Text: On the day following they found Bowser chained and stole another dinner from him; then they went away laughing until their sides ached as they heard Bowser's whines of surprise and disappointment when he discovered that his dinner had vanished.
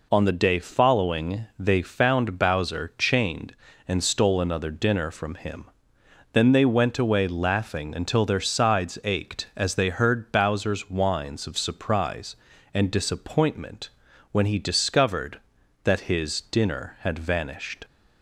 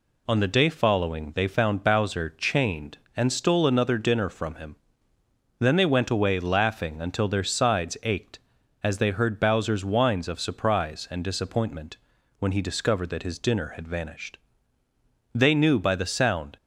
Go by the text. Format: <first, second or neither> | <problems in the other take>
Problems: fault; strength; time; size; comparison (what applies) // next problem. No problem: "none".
first | pauses between "disappointment" and "when"; at 11.9 s; 0.42 s long; also in the first // goes on to say "They knew by the sound"; noticeable; from 15.3 s on; 1.2 s long